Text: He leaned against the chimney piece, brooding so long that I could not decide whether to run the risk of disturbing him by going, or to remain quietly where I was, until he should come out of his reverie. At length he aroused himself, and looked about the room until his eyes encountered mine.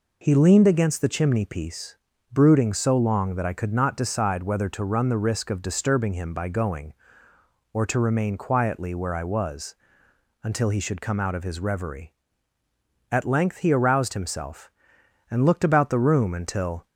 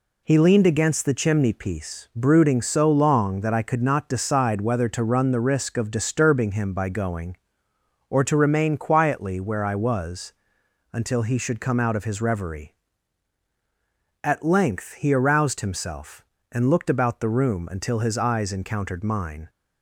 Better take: second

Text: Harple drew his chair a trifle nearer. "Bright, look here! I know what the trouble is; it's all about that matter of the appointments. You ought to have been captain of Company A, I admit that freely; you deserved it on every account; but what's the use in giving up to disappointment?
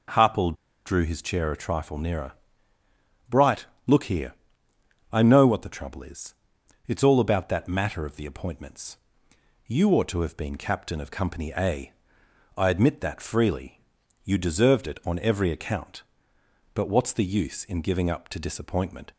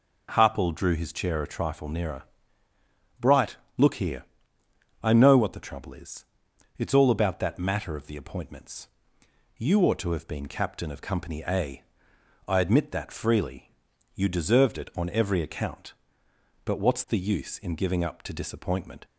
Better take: second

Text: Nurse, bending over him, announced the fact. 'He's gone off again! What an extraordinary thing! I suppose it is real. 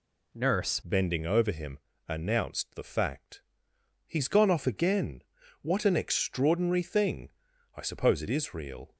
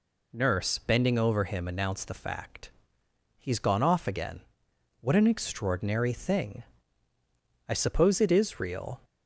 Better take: second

